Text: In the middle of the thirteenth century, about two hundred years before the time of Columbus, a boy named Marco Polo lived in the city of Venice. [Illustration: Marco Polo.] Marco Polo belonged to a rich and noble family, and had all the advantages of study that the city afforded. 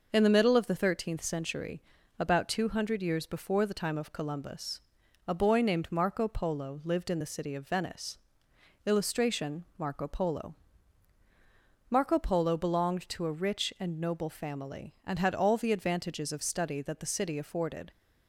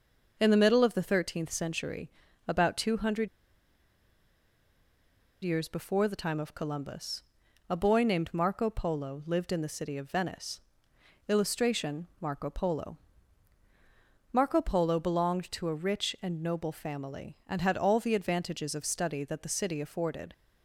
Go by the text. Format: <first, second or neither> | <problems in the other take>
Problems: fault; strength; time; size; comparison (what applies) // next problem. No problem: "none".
first | pauses between "hundred" and "years"; strong; at 3.2 s; 2.1 s long